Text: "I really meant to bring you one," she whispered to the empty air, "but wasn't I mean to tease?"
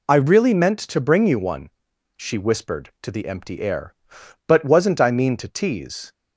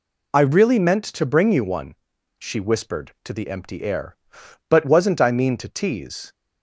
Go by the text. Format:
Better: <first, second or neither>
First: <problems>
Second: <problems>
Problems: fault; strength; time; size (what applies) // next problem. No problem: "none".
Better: neither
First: none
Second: none